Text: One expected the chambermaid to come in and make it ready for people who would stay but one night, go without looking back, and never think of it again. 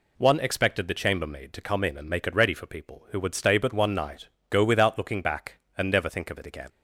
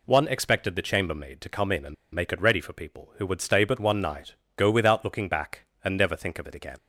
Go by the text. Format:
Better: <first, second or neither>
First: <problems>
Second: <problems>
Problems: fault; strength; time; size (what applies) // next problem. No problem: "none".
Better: first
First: none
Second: pauses between "and" and "make"; slight; at 1.9 s; 0.19 s long